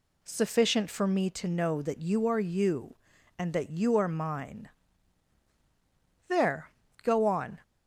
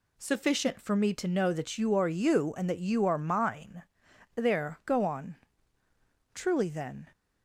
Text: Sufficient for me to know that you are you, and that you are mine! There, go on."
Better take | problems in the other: first | goes on to say "Truly then"; noticeable; from 6.3 s on; 0.76 s long

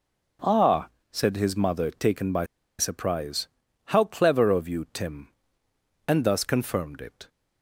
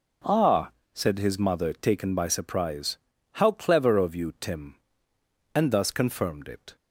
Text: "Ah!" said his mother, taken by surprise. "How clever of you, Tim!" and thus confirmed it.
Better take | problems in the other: second | pauses between "by" and "surprise"; slight; at 2.4 s; 0.32 s long

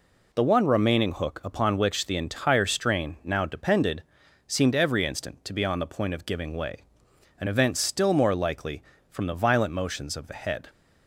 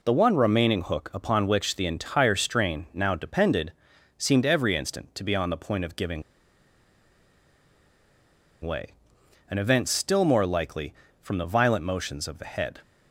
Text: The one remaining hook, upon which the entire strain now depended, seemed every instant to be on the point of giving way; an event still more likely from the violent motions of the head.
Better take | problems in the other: first | pauses between "giving" and "way"; strong; at 6.2 s; 2.4 s long

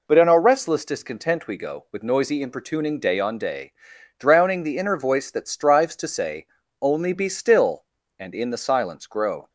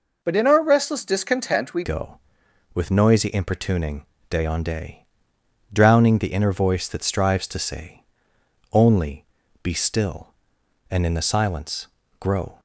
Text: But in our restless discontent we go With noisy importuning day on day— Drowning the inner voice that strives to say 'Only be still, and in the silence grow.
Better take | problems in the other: first | changes voice at "go"; from 1.8 s on; 10.7 s long // pauses between "importuning" and "day"; slight; at 4.0 s; 0.24 s long // pauses between "say" and "Only"; noticeable; at 8.0 s; 0.70 s long; also in the first // pauses between "Only" and "be"; at 9.2 s; 0.38 s long // pauses between "silence" and "grow"; slight; at 11.8 s; 0.32 s long

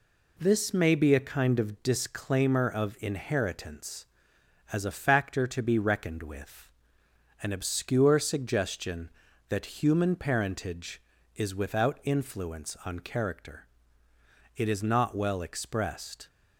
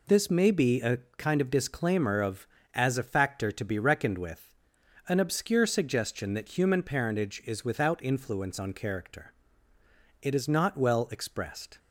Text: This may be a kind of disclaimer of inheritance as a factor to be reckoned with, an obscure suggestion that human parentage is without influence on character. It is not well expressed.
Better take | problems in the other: first | pauses between "a" and "kind"; slight; at 0.9 s; 0.20 s long // skips "inheritance"; at 2.5 s

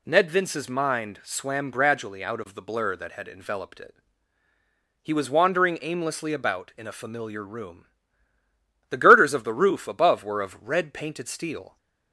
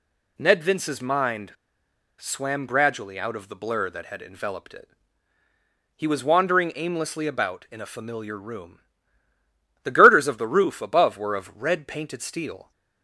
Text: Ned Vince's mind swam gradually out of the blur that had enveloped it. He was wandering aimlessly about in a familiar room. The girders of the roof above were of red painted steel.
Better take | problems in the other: first | pauses between "mind" and "swam"; noticeable; at 1.5 s; 0.66 s long

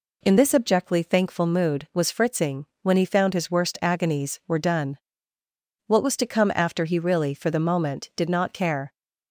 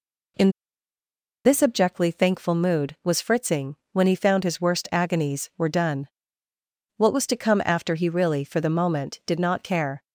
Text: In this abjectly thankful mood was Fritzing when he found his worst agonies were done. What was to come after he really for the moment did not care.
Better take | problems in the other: first | pauses between "In" and "this"; noticeable; at 0.5 s; 0.94 s long // pauses between "Fritzing" and "when"; slight; at 3.7 s; 0.16 s long; slight in the first

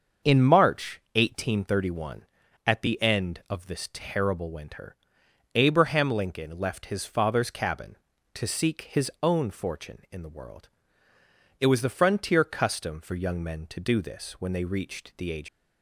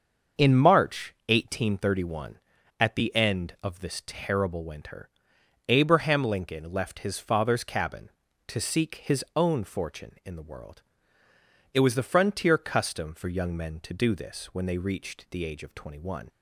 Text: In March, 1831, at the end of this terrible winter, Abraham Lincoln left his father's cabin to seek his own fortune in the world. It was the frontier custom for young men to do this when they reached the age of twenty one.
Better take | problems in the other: second | starts louder than the rest; until 1.3 s; 6.5 dB; also in the second // stops before "of twenty one"; at 15.4 s

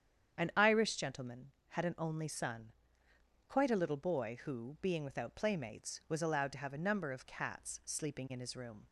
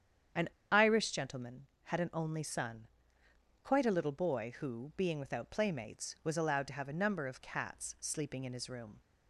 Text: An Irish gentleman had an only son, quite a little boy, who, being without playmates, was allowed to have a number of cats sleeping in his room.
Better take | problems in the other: first | starts louder than the rest; strong; until 1.5 s; 8.5 dB; strong in the first // pauses between "An" and "Irish"; slight; at 0.4 s; 0.23 s long

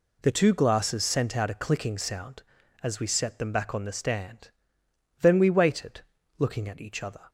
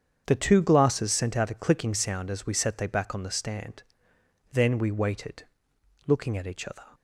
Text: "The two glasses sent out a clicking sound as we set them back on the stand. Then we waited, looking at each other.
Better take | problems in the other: first | starts louder than the rest; strong; until 1.2 s; 7.5 dB // says "they" for "them"; at 2.7 s

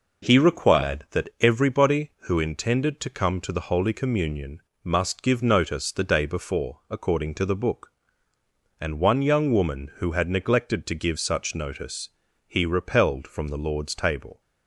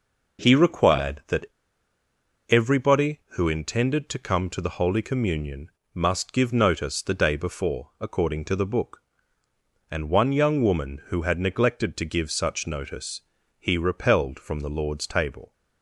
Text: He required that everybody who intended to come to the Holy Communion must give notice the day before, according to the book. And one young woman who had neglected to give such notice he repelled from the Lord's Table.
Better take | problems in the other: first | pauses between "that" and "everybody"; at 1.4 s; 1.0 s long // pauses between "Communion" and "must"; slight; at 5.7 s; 0.24 s long; slight in the first // pauses between "notice" and "he"; slight; at 13.2 s; 0.36 s long; slight in the first

